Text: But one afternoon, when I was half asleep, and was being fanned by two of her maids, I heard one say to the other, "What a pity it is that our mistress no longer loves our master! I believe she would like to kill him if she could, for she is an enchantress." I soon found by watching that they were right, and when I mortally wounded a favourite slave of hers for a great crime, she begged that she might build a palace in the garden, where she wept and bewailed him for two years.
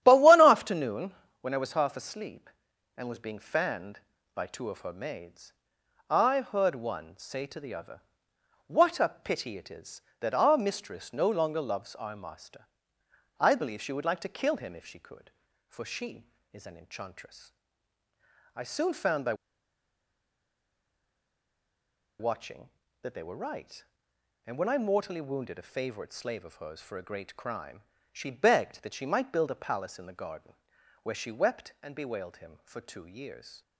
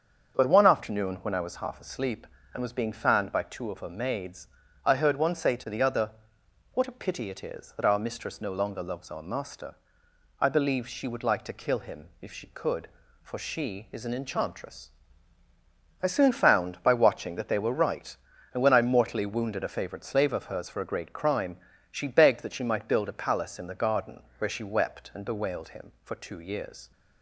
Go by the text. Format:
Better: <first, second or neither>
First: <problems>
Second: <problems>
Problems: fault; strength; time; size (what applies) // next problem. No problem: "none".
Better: second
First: starts louder than the rest; strong; until 1.0 s; 11 dB // pauses between "by" and "watching"; strong; at 19.3 s; 2.8 s long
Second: starts louder than the rest; strong; until 1.3 s; 7 dB